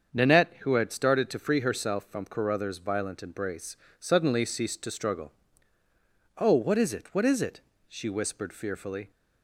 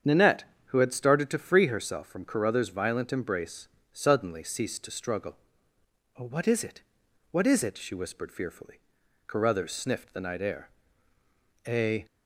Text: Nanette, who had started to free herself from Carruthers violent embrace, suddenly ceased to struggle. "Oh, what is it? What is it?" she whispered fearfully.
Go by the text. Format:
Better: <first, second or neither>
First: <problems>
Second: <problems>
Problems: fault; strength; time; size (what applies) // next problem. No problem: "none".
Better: first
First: starts louder than the rest; until 1.1 s; 7 dB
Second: starts louder than the rest; strong; until 1.2 s; 7.5 dB // goes on to say "Carruthers sniffed the night air A"; strong; from 9.2 s on; 2.7 s long